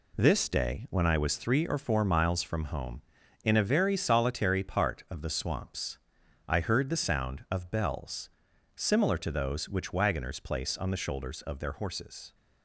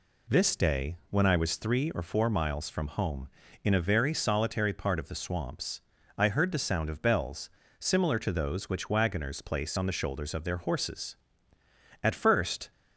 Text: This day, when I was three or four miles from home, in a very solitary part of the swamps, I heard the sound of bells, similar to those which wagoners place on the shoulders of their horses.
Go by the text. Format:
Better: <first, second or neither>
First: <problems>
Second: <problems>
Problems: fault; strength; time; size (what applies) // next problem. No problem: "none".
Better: first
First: none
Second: goes on to say "At first"; noticeable; from 12.0 s on; 0.68 s long